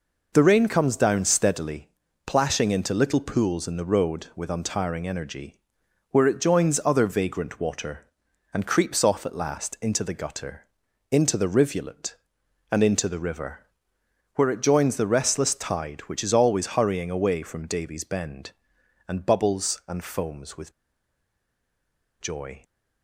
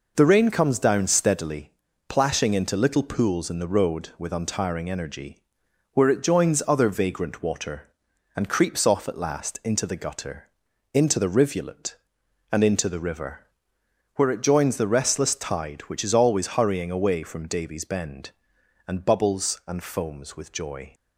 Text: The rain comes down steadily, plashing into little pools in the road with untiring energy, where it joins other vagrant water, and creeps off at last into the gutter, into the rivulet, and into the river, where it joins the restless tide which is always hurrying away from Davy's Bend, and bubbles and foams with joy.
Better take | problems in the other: second | pauses between "with" and "joy"; strong; at 20.7 s; 1.4 s long

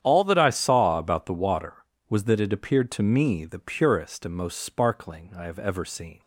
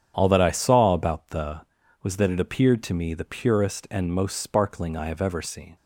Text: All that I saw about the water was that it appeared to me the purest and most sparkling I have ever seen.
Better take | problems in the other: first | starts louder than the rest; strong; until 1.1 s; 9 dB; strong in the first // skips "water"; at 1.8 s

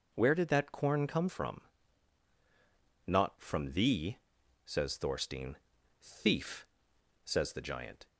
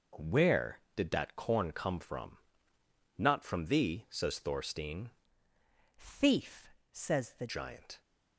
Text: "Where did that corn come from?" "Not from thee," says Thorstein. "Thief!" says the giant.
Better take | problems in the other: first | changes voice from "Thief" to "the"; from 5.9 to 7.4 s; 1.5 s long

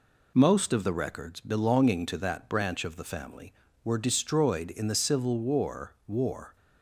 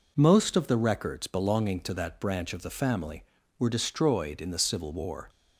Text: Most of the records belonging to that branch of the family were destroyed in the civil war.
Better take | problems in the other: second | says "war" twice; at 6.0 s

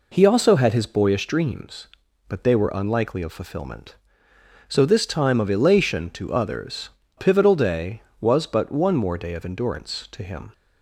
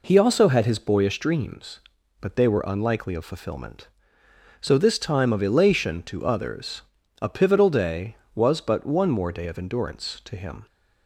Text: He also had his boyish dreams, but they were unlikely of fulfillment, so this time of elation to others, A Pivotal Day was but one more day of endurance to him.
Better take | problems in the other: second | skips "A"; at 7.0 s

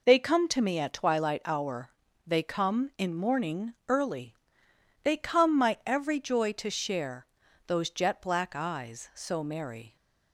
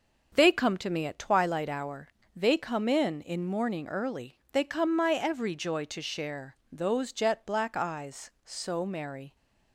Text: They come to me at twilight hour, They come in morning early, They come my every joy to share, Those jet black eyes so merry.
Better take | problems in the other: first | says "in" twice; at 3.2 s

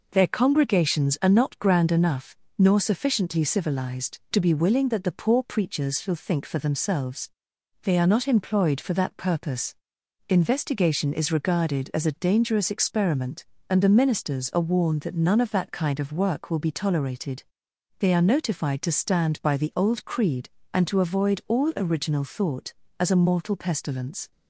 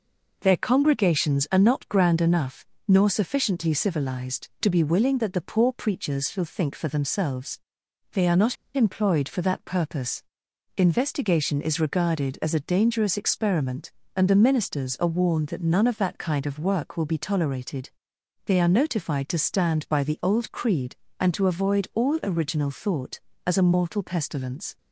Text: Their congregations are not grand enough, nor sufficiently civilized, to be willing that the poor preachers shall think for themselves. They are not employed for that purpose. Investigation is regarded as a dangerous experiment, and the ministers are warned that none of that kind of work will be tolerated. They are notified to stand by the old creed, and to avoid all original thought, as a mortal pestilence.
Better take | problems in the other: first | pauses between "not" and "employed"; slight; at 8.5 s; 0.19 s long

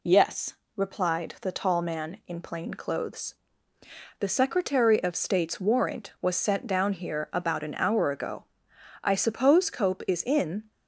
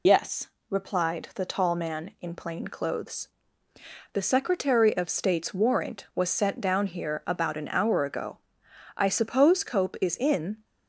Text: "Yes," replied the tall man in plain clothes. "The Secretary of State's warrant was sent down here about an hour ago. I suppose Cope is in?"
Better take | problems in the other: first | loses the start of "Yes"; at 0.0 s; 95 ms

